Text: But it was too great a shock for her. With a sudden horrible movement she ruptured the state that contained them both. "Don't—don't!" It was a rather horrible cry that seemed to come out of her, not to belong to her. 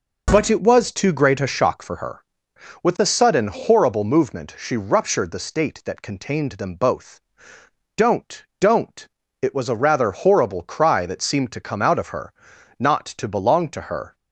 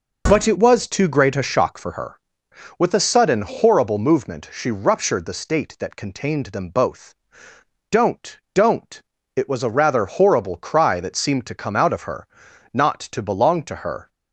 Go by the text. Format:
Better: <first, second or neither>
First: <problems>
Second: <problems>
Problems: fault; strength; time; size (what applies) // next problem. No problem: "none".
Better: neither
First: none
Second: none